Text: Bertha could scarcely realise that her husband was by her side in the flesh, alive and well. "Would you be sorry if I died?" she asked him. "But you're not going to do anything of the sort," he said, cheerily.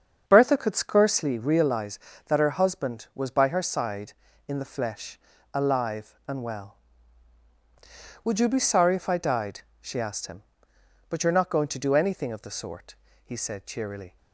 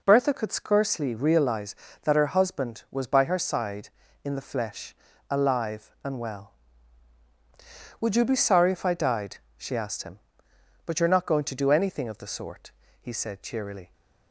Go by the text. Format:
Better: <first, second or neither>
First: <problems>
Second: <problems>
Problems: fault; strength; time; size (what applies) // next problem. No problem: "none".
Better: second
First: starts louder than the rest; strong; until 1.4 s; 7.5 dB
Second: none